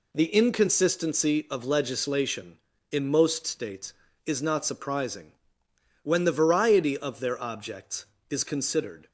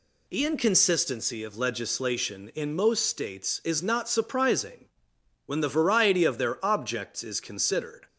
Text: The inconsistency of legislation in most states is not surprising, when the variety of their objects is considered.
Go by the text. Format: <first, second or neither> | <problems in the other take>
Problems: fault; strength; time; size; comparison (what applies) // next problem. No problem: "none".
neither | none